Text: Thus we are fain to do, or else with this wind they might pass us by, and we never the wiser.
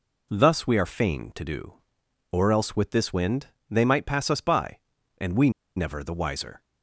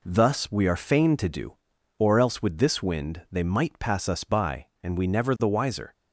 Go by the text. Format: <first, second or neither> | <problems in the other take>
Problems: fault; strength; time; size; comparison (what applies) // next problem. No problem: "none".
second | pauses between "wind" and "they"; slight; at 3.4 s; 0.20 s long // pauses between "we" and "never"; slight; at 5.4 s; 0.26 s long